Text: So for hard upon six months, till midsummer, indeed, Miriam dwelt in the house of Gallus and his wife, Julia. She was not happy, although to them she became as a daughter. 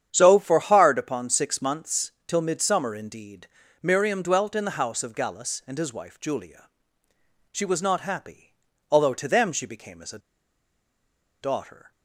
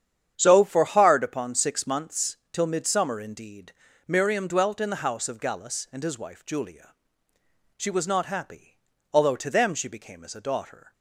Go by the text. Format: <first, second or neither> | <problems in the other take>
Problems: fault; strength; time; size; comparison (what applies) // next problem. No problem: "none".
second | starts louder than the rest; strong; until 1.1 s; 9 dB; strong in the second // pauses between "a" and "daughter"; at 10.1 s; 1.2 s long